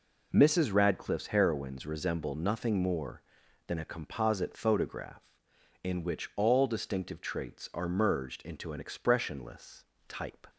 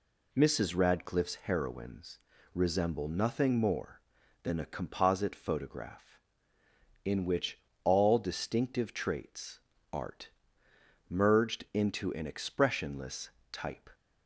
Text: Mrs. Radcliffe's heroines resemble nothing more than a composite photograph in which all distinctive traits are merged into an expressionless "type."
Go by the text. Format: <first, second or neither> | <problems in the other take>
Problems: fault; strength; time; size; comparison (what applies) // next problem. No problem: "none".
first | pauses between "heroines" and "resemble"; slight; at 2.1 s; 0.36 s long // pauses between "which" and "all"; slight; at 7.5 s; 0.24 s long // says "art" for "are"; at 9.9 s // pauses between "expressionless" and "type"; slight; at 13.3 s; 0.20 s long; slight in the first